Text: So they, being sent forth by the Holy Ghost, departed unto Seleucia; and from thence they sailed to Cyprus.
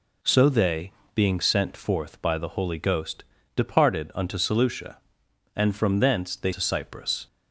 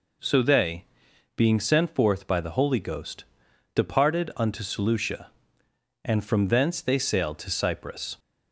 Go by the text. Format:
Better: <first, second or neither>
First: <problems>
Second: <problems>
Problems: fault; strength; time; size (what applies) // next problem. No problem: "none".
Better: second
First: skips "sailed"; at 6.5 s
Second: none